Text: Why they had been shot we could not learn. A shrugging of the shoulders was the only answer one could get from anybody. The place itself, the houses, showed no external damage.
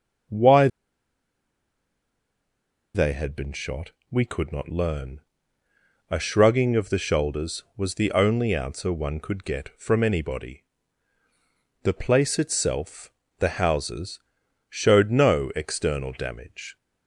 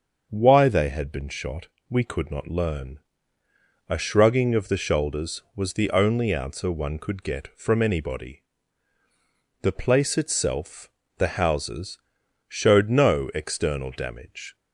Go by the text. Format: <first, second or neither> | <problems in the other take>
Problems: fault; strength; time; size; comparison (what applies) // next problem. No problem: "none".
second | starts louder than the rest; until 3.5 s; 6.5 dB; also in the second // pauses between "Why" and "they"; strong; at 0.6 s; 2.2 s long // pauses between "shot" and "we"; slight; at 3.9 s; 0.18 s long; slight in the second